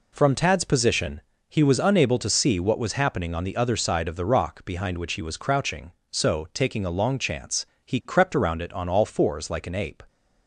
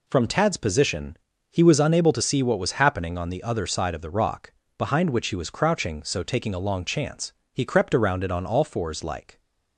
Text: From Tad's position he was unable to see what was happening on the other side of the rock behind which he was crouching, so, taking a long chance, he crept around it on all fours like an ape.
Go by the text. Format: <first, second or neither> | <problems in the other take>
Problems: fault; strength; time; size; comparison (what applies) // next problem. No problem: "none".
first | pauses between "position" and "he"; slight; at 1.1 s; 0.34 s long; slight in the first // pauses between "rock" and "behind"; slight; at 4.5 s; 0.24 s long // stops before "an ape"; at 9.3 s